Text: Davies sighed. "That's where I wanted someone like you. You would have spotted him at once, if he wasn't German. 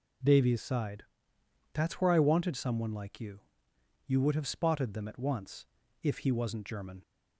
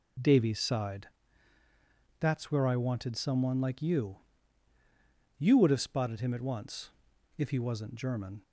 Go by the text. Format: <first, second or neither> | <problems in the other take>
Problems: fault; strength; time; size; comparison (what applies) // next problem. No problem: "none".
second | says "them" for "him"; at 4.9 s